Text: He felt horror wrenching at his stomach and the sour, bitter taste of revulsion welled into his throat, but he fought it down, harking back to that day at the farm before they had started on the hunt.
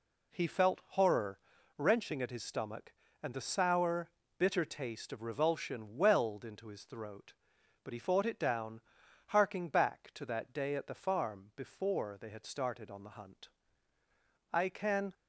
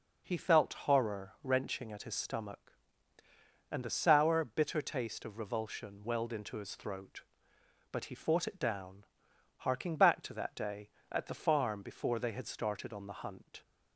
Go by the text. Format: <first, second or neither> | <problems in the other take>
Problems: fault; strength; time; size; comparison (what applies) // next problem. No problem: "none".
second | pauses between "horror" and "wrenching"; at 1.3 s; 0.40 s long // goes on to say "I can"; from 14.5 s on; 0.60 s long